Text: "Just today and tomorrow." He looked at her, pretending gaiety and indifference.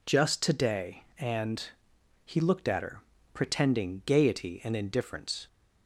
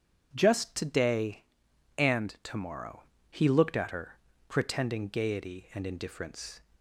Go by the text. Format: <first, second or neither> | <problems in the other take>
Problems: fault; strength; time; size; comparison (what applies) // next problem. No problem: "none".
second | skips "tomorrow"; at 1.9 s